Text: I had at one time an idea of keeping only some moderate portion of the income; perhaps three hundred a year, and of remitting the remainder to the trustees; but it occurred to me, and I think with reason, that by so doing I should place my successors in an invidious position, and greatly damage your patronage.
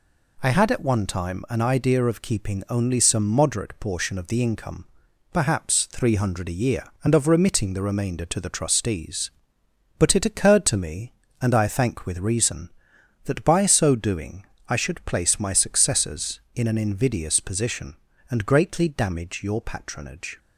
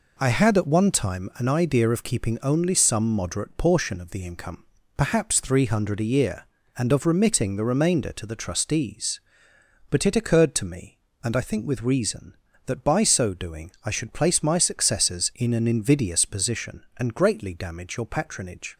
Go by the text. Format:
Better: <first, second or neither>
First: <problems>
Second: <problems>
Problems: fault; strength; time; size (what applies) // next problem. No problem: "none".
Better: second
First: says "thank" for "think"; at 11.6 s // pauses between "doing" and "I"; slight; at 14.4 s; 0.22 s long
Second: none